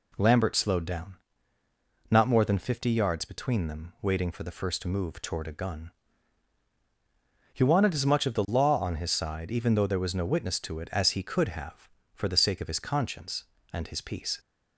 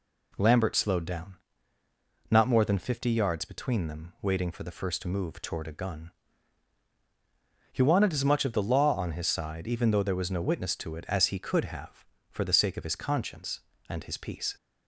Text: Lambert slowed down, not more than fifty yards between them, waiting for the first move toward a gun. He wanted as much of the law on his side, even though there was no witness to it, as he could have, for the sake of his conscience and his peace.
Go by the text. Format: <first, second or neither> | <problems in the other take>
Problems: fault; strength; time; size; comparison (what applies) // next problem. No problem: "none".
neither | none